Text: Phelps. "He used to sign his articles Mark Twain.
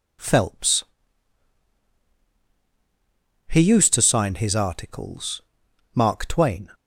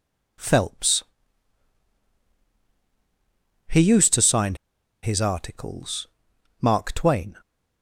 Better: first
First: pauses between "articles" and "Mark"; noticeable; at 5.4 s; 0.53 s long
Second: pauses between "sign" and "his"; noticeable; at 4.5 s; 0.47 s long // pauses between "articles" and "Mark"; noticeable; at 6.0 s; 0.54 s long

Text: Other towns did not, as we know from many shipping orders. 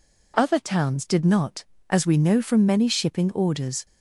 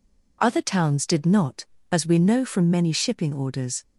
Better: neither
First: none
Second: none

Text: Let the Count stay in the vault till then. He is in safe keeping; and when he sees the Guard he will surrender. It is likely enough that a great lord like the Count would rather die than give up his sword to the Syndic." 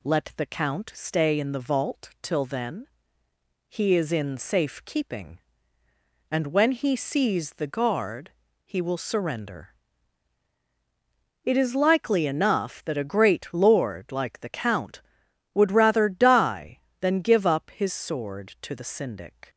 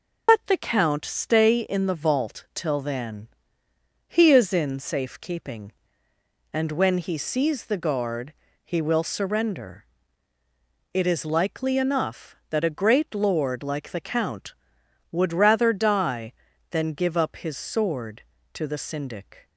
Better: first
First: pauses between "Guard" and "he"; slight; at 8.3 s; 0.34 s long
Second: loses the start of "Let"; at 0.2 s; 125 ms // pauses between "Guard" and "he"; slight; at 8.3 s; 0.32 s long

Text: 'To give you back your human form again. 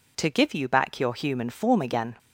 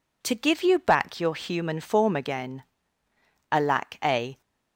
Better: first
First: none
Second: goes on to say "Alack a"; noticeable; from 3.5 s on; 0.90 s long

